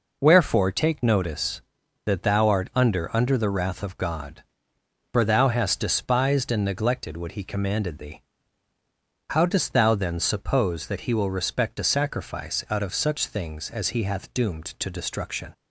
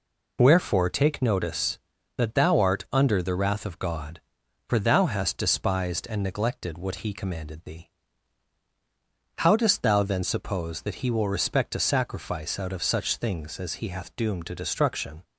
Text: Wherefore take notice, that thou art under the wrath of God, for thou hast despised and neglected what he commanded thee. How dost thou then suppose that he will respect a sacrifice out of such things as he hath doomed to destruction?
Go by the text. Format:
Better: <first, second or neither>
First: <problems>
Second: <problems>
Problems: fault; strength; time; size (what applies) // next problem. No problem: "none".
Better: second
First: says "under" twice; at 3.1 s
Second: none